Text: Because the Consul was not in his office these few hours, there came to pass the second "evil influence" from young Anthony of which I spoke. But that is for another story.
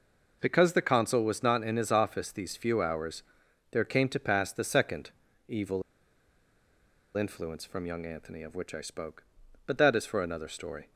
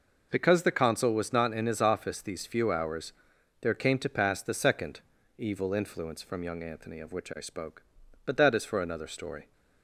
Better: second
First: pauses between "second" and "evil"; at 5.1 s; 0.38 s long // pauses between "evil" and "influence"; strong; at 5.8 s; 1.3 s long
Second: pauses between "second" and "evil"; at 4.9 s; 0.38 s long

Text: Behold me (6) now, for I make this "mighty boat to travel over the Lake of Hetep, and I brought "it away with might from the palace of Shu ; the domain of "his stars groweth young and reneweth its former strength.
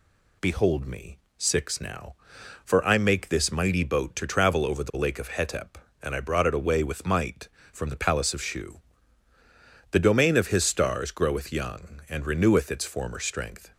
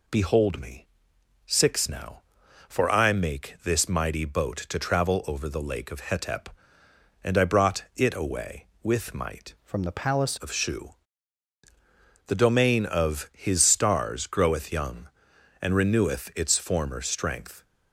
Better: first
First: none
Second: changes voice from "from" to "palace"; from 9.6 to 10.3 s; 0.7 s long

